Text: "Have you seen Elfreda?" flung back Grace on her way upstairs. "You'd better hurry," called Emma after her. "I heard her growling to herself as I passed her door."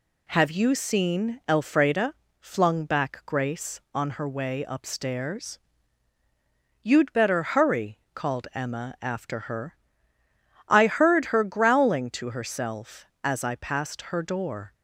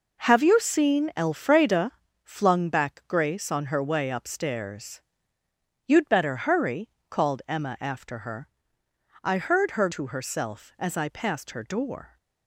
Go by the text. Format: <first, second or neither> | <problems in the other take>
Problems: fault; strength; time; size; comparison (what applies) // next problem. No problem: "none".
first | skips "growling"; at 9.8 s